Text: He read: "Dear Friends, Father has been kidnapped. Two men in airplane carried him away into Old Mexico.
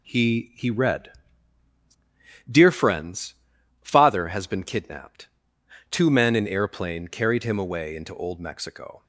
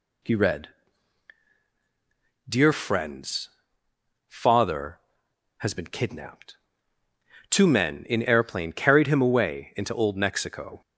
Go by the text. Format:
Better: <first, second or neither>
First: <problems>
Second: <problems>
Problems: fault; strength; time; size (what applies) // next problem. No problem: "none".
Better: second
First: says "He" twice; at 0.5 s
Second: none